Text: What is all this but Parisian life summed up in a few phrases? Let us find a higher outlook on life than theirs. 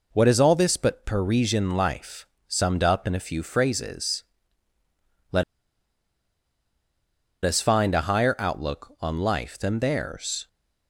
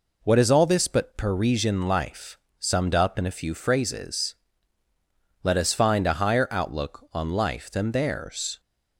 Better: second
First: pauses between "life" and "summed"; slight; at 2.2 s; 0.22 s long // pauses between "Let" and "us"; strong; at 5.4 s; 2.0 s long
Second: pauses between "life" and "summed"; slight; at 2.3 s; 0.22 s long

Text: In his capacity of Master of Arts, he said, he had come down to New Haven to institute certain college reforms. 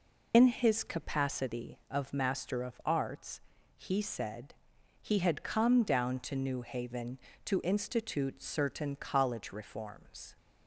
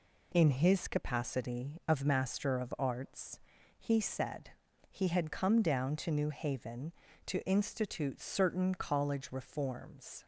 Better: second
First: loses the start of "In"; at 0.3 s; 65 ms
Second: none

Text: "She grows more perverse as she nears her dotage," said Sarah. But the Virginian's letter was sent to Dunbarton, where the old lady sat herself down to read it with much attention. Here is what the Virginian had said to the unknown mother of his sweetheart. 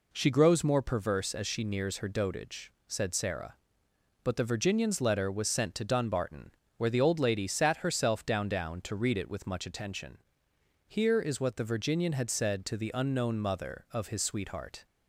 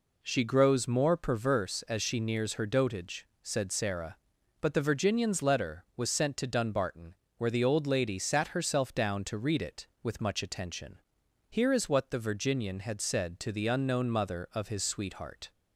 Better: second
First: says "down" twice; at 8.4 s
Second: none

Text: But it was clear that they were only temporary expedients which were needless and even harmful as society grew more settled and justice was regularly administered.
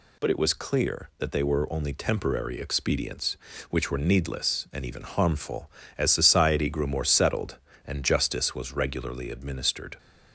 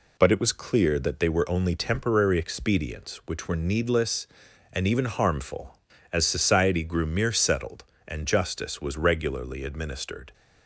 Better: first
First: none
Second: says "mere" for "more"; at 7.0 s

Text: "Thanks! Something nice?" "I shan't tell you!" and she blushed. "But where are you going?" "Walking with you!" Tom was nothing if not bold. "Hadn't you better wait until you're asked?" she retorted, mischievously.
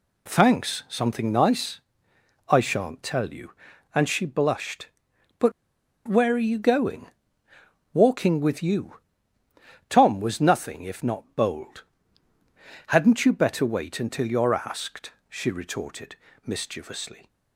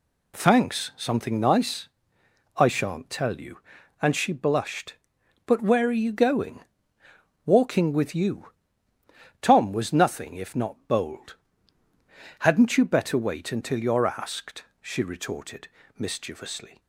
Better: second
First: pauses between "But" and "where"; noticeable; at 5.5 s; 0.56 s long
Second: none

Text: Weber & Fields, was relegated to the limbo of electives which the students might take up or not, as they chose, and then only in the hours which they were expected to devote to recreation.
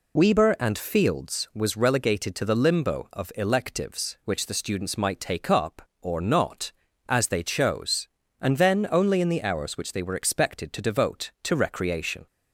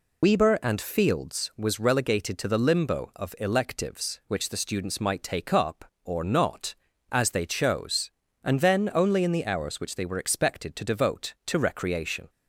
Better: first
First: none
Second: loses the start of "Weber"; at 0.2 s; 45 ms

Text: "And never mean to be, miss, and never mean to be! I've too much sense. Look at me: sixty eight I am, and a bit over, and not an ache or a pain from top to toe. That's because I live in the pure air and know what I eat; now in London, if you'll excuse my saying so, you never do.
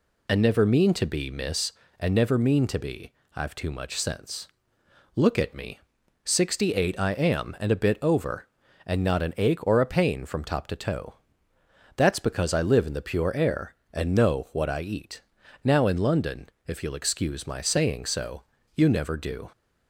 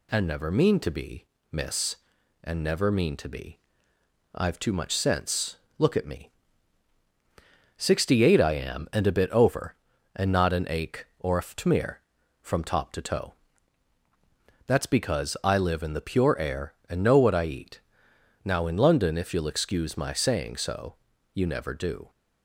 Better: first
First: none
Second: says "ftmir" for "pain"; at 11.4 s

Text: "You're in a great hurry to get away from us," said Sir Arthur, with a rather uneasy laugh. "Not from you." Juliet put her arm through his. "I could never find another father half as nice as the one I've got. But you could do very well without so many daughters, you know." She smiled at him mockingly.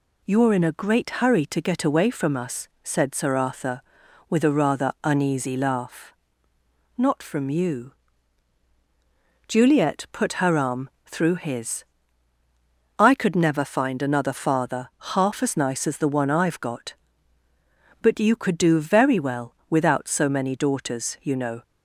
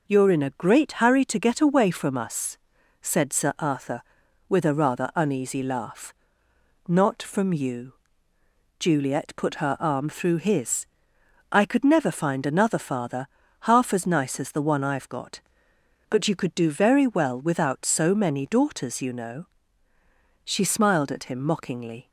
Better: second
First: pauses between "arm" and "through"; slight; at 10.8 s; 0.18 s long // pauses between "father" and "half"; slight; at 14.8 s; 0.24 s long // stops before "She smiled at him mockingly"; at 21.6 s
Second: pauses between "father" and "half"; slight; at 13.2 s; 0.34 s long

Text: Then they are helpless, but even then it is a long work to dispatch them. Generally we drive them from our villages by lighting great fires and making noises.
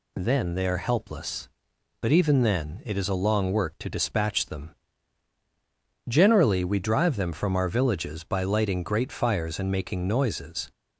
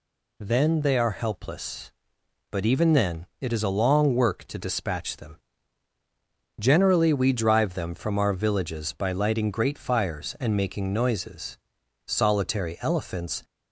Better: first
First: none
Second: goes on to say "Solitary elephants"; from 12.0 s on; 1.3 s long

